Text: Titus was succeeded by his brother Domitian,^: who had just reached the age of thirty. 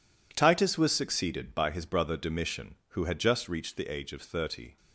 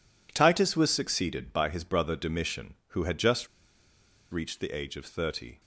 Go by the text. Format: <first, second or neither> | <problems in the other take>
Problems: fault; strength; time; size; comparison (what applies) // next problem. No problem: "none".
first | pauses between "just" and "reached"; noticeable; at 3.4 s; 0.84 s long